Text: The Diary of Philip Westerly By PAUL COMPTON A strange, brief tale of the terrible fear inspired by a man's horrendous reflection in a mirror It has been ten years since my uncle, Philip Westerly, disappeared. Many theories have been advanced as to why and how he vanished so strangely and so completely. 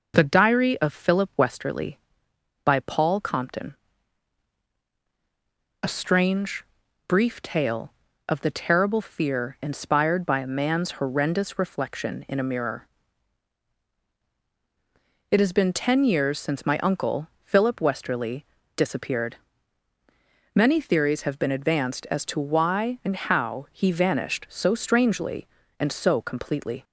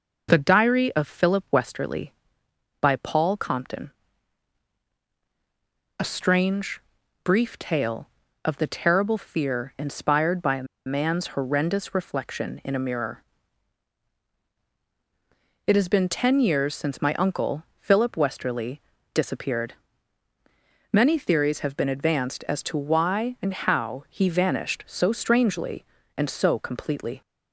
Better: first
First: pauses between "COMPTON" and "A"; strong; at 3.7 s; 2.0 s long // pauses between "mirror" and "It"; strong; at 12.8 s; 2.4 s long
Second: pauses between "COMPTON" and "A"; strong; at 3.8 s; 2.0 s long // pauses between "a" and "man's"; slight; at 10.6 s; 0.22 s long // pauses between "mirror" and "It"; strong; at 13.2 s; 2.4 s long

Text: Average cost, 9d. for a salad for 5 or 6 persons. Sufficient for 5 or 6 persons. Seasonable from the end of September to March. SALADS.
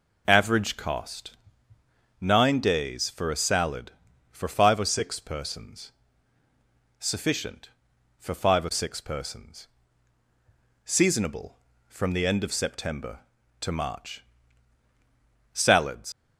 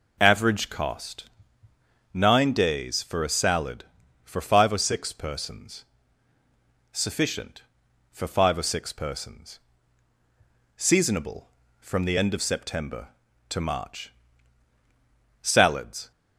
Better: second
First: leaves "SALADS" unfinished; at 16.1 s; 100 ms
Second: none

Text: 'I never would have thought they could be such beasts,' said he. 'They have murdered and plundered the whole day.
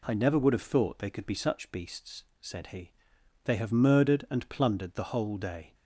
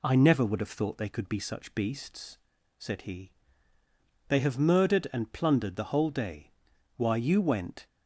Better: first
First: none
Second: goes on to say "Why you went"; noticeable; from 6.9 s on; 0.90 s long

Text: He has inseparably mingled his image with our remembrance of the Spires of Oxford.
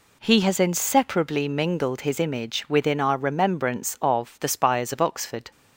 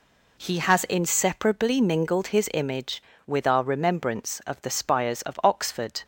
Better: second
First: says "within" for "with"; at 2.6 s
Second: none

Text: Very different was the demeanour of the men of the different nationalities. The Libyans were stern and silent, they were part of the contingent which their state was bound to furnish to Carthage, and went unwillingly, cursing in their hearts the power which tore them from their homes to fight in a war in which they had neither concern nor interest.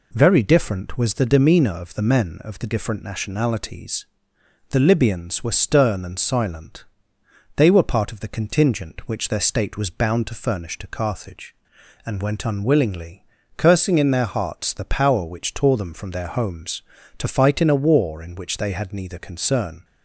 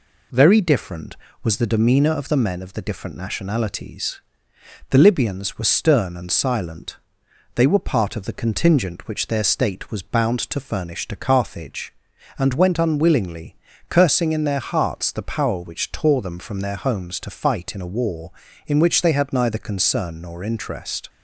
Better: second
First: stops before "nor interest"; at 19.8 s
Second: none

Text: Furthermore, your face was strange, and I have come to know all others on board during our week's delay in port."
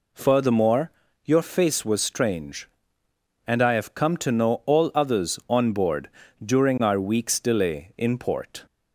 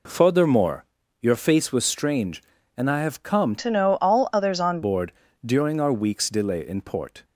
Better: first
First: pauses between "board" and "during"; slight; at 6.0 s; 0.36 s long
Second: changes voice from "to" to "on"; from 3.5 to 4.8 s; 1.3 s long // pauses between "board" and "during"; slight; at 5.1 s; 0.32 s long

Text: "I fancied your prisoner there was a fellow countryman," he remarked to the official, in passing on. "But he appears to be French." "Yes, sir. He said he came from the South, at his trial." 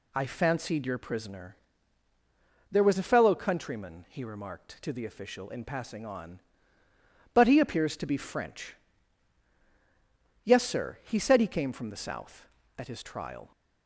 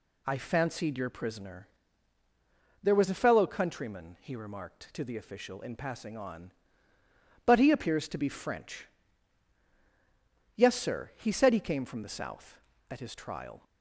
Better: neither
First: pauses between "prisoner" and "there"; at 1.5 s; 1.1 s long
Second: pauses between "prisoner" and "there"; at 1.6 s; 1.1 s long

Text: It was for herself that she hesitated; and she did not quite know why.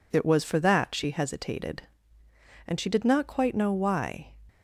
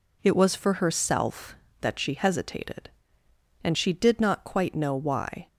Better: second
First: skips "herself"; at 0.5 s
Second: none

